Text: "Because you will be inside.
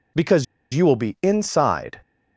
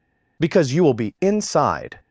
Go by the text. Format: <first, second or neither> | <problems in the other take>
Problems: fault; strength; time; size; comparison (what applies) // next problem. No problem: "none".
second | pauses between "Because" and "you"; slight; at 0.4 s; 0.28 s long